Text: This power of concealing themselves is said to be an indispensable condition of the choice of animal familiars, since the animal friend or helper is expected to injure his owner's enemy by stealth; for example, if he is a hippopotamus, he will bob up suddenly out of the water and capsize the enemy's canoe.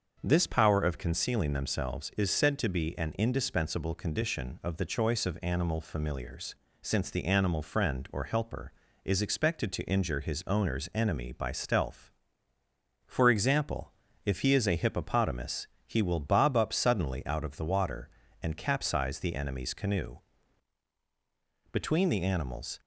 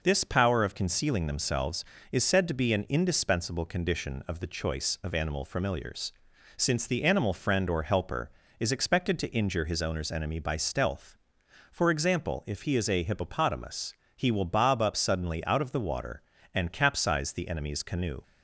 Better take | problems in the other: second | starts louder than the rest; until 1.2 s; 6.5 dB // goes on to say "Between the animals"; noticeable; from 21.7 s on; 1.0 s long

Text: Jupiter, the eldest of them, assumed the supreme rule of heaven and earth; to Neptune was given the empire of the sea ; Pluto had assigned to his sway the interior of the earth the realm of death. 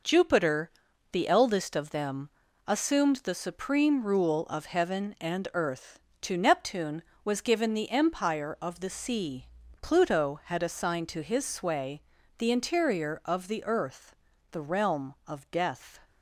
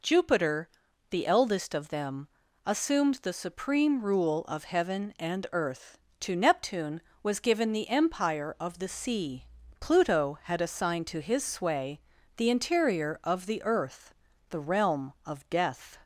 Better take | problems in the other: second | gets quieter; throughout; 6.5 dB // pauses between "sway" and "the"; slight; at 12.0 s; 0.36 s long; slight in the second // pauses between "earth" and "the"; slight; at 14.1 s; 0.36 s long; slight in the second

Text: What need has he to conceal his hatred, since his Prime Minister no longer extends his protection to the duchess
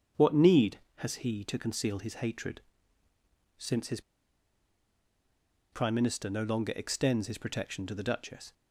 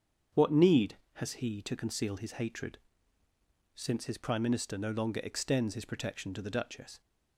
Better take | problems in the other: second | starts louder than the rest; strong; until 1.3 s; 7.5 dB; strong in the second // pauses between "his" and "Prime"; strong; at 3.9 s; 1.7 s long

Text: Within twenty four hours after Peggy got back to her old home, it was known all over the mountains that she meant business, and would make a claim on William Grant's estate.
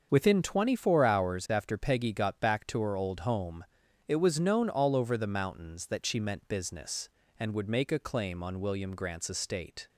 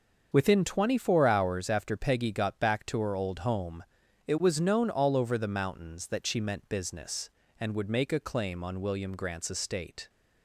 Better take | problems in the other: neither | starts louder than the rest; the same in both

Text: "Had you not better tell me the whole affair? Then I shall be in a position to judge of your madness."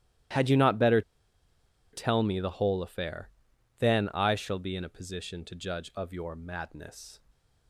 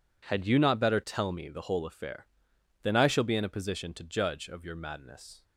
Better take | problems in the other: second | starts louder than the rest; strong; until 2.2 s; 14 dB // pauses between "better" and "tell"; noticeable; at 1.0 s; 0.91 s long

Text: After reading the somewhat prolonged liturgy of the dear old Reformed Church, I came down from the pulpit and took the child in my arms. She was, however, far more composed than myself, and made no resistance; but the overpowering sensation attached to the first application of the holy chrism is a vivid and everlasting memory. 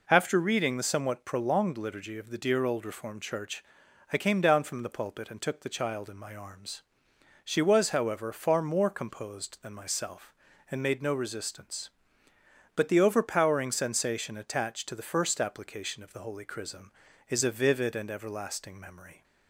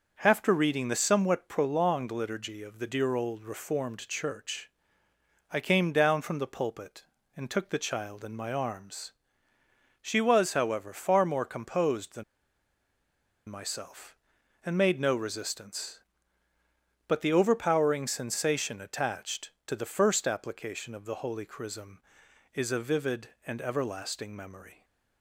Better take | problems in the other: first | pauses between "than" and "myself"; at 12.2 s; 1.2 s long

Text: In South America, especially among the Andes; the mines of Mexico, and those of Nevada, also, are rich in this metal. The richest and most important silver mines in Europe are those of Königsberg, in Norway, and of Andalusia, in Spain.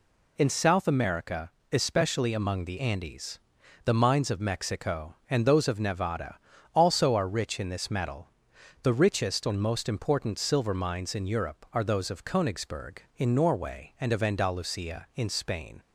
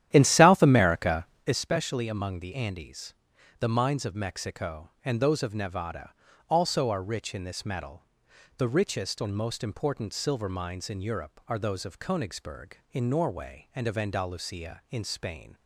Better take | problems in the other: first | starts louder than the rest; strong; until 1.6 s; 11.5 dB

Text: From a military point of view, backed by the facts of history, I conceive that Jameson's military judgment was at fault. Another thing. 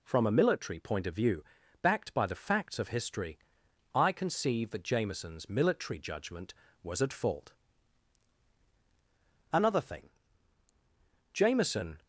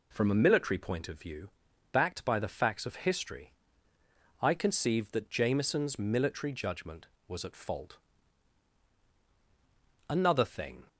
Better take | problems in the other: second | goes on to say "Jameson"; noticeable; from 11.3 s on; 0.70 s long

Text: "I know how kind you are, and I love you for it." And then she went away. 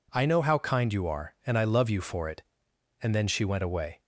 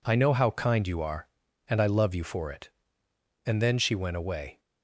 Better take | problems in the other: neither | none

